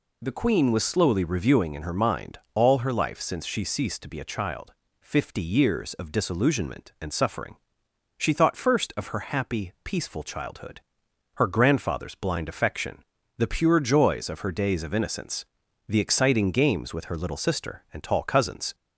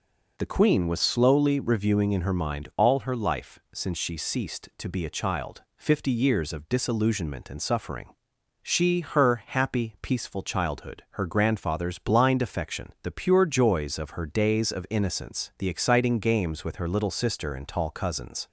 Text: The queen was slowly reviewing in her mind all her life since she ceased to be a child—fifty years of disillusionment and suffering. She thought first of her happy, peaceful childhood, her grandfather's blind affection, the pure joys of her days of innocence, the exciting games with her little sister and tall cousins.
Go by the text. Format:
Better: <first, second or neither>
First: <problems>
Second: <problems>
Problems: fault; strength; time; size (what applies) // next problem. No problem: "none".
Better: first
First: none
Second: skips "thought first of"; at 9.0 s